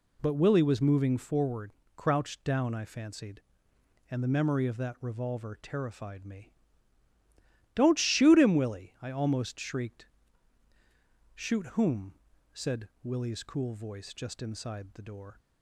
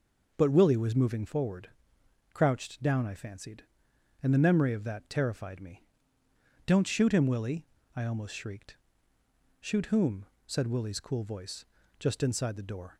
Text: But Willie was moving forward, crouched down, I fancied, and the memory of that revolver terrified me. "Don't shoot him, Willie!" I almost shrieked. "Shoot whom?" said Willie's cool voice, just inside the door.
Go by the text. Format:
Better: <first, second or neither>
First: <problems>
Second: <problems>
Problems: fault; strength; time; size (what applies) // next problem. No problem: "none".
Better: first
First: none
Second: skips "revolver"; at 5.0 s